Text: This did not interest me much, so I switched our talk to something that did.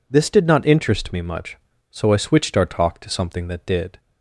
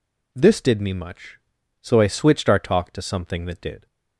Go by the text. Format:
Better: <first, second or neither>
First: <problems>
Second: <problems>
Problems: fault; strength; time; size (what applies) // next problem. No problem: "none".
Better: first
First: none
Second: skips "not interest"; at 0.7 s